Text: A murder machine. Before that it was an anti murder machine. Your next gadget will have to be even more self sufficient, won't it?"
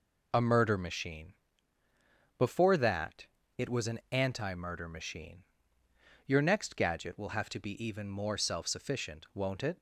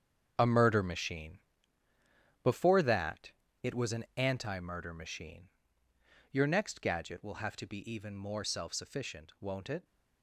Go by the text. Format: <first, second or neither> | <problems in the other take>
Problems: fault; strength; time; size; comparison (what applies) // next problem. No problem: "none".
first | gets quieter; strong; throughout; 10 dB // pauses between "that" and "it"; slight; at 3.3 s; 0.28 s long; slight in the first